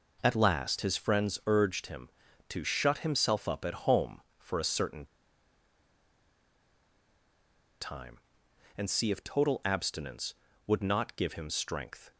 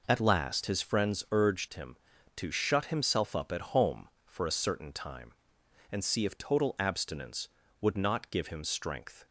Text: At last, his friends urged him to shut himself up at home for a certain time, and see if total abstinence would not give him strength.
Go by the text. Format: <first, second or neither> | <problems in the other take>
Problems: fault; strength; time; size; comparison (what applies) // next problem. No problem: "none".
second | pauses between "certain" and "time"; strong; at 5.0 s; 2.7 s long